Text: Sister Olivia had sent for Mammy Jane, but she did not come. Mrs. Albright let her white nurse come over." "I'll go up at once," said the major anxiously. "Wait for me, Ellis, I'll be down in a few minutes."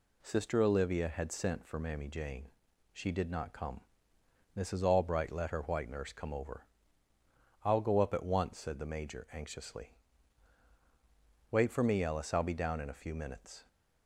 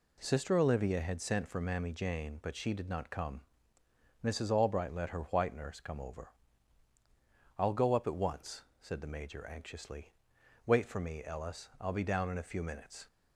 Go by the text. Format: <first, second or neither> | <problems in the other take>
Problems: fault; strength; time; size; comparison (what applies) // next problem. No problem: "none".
second | skips "but"; at 2.7 s